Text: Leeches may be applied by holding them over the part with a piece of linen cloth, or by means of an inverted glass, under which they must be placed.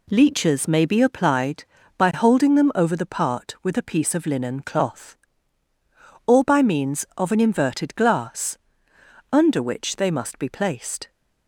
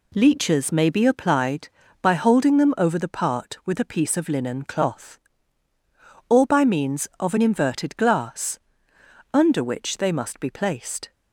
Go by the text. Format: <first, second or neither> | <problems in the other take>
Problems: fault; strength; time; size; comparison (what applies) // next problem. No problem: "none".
neither | none